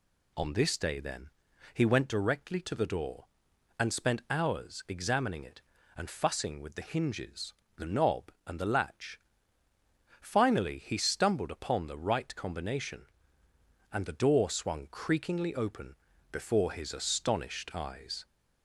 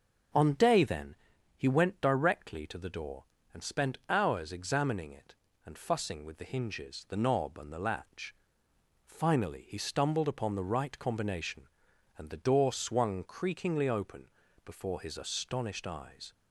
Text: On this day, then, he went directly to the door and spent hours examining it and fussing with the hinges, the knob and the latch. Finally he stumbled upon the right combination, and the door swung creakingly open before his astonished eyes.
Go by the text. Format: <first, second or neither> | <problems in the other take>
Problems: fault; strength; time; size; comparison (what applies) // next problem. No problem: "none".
first | starts louder than the rest; noticeable; until 1.7 s; 6 dB // skips "this"; at 0.5 s // pauses between "open" and "before"; at 14.2 s; 0.38 s long; slight in the first